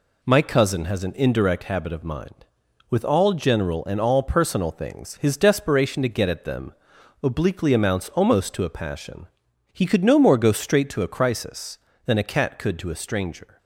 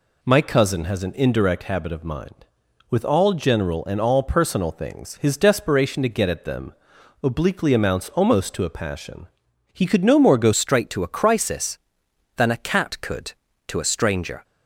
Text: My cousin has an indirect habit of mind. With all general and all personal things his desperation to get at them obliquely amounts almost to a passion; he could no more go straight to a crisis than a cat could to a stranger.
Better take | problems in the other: first | pauses between "them" and "obliquely"; noticeable; at 6.7 s; 0.50 s long; noticeable in the first // changes voice at "straight"; from 10.5 s on; 3.9 s long

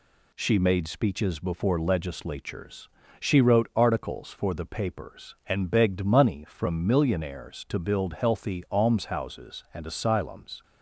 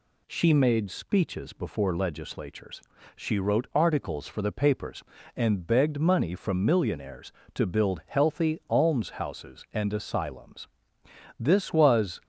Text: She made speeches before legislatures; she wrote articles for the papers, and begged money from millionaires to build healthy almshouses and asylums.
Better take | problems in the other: first | goes on to say "This was"; noticeable; from 11.3 s on; 0.84 s long

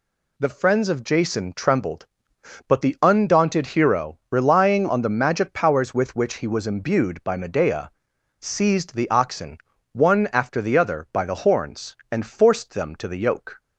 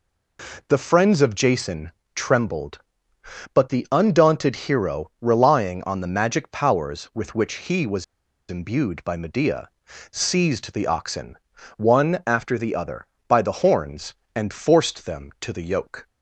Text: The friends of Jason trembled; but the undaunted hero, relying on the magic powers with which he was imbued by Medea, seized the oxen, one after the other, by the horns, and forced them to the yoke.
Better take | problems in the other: first | pauses between "Jason" and "trembled"; slight; at 1.9 s; 0.22 s long // pauses between "was" and "imbued"; at 8.0 s; 0.45 s long

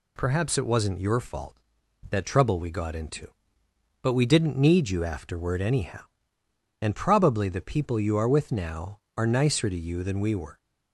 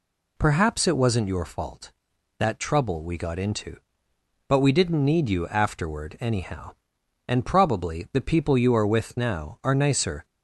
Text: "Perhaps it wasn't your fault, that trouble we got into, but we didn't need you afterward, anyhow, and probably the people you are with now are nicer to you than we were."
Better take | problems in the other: first | stops before "to you than we were"; at 10.2 s

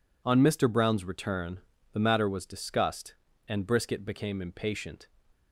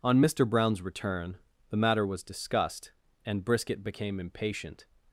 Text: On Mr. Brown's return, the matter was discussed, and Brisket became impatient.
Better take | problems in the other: neither | none

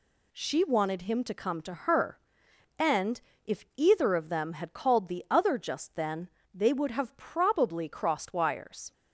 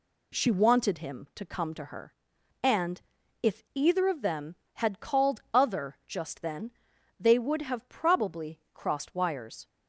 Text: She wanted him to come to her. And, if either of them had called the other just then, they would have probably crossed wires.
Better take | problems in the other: first | skips "the"; at 5.4 s // pauses between "probably" and "crossed"; slight; at 8.5 s; 0.16 s long

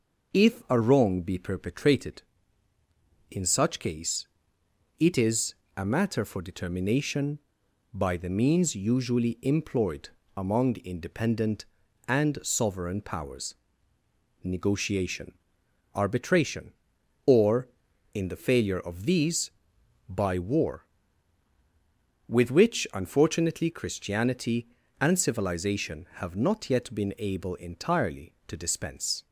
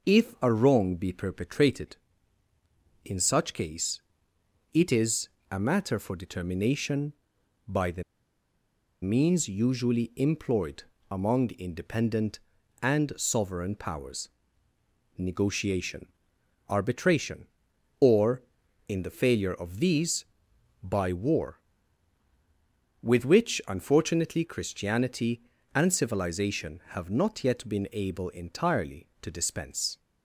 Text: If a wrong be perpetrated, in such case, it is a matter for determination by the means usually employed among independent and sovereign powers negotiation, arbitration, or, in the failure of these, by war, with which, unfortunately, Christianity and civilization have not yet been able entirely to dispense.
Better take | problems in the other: first | pauses between "is" and "a"; slight; at 5.2 s; 0.22 s long; slight in the first // pauses between "the" and "means"; at 8.0 s; 0.99 s long // pauses between "employed" and "among"; slight; at 10.8 s; 0.28 s long; slight in the first // pauses between "powers" and "negotiation"; noticeable; at 14.2 s; 0.88 s long; noticeable in the first

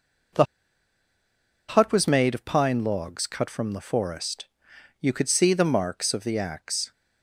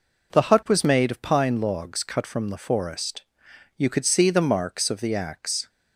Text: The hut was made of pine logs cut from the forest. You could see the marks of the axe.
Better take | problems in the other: second | pauses between "The" and "hut"; at 0.4 s; 1.2 s long

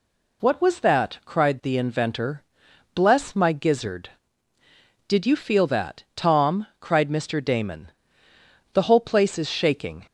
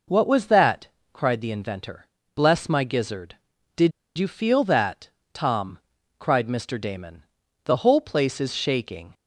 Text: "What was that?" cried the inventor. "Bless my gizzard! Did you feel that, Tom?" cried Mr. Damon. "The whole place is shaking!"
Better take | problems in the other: first | pauses between "Did" and "you"; slight; at 3.9 s; 0.26 s long

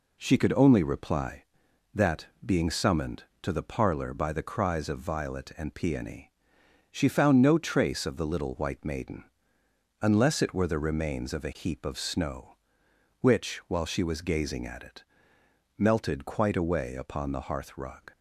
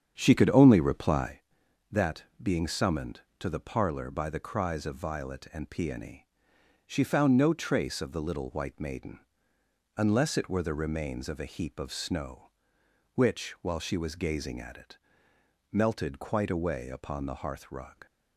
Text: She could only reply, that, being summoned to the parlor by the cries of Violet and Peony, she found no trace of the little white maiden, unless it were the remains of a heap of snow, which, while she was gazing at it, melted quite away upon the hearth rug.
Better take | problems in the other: first | starts louder than the rest; strong; until 1.4 s; 8 dB

